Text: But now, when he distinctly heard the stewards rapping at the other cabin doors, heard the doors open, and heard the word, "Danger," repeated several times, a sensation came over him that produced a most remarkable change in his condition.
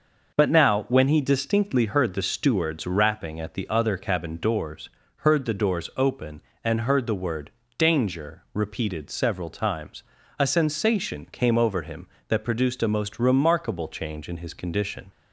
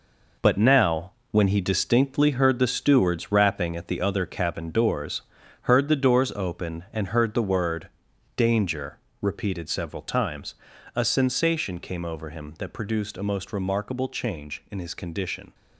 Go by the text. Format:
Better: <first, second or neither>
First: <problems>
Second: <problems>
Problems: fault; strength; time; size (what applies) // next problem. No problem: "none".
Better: first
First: none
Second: gets quieter; throughout; 7 dB